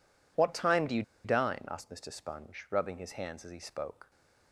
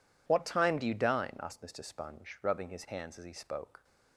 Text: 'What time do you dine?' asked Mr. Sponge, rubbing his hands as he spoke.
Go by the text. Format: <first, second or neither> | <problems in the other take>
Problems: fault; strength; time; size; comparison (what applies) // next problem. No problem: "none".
second | pauses between "you" and "dine"; slight; at 1.0 s; 0.22 s long